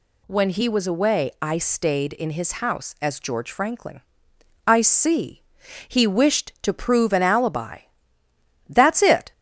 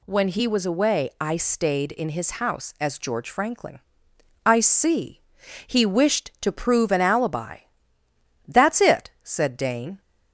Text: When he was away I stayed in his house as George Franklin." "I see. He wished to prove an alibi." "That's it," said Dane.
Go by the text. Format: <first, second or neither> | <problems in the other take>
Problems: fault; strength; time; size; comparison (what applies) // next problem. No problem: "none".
second | stops before "said Dane"; at 9.3 s